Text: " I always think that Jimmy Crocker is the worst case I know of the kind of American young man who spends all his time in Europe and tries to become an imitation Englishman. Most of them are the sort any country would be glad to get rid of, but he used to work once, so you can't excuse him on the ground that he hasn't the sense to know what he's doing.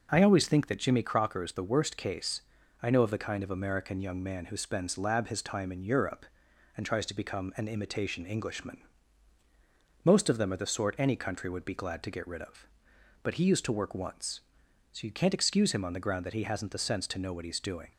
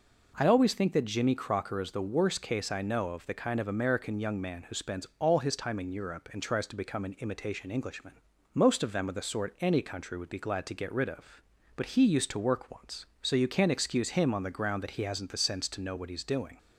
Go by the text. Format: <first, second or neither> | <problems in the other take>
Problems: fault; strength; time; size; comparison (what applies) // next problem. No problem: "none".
second | pauses between "case" and "I"; at 2.4 s; 0.40 s long // says "lab" for "all"; at 4.9 s